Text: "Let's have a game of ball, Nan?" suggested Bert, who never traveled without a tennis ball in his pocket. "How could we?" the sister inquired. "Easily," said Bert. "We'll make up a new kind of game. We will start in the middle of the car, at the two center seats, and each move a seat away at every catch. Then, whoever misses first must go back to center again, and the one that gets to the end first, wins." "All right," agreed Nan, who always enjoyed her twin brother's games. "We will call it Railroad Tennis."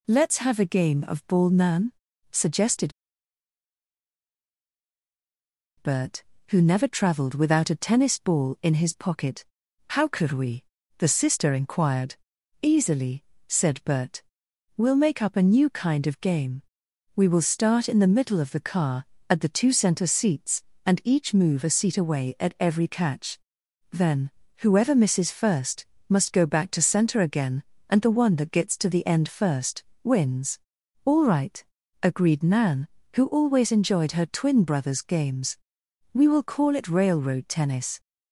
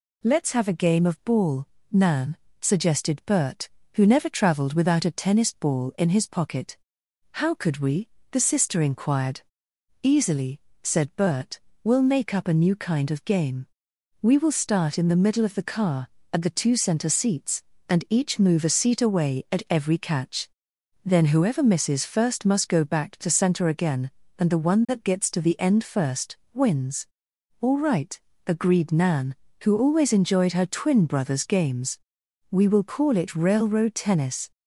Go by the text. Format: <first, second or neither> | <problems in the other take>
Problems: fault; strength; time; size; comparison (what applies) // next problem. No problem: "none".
second | pauses between "suggested" and "Bert"; strong; at 2.9 s; 2.8 s long // pauses between "first" and "must"; slight; at 25.8 s; 0.24 s long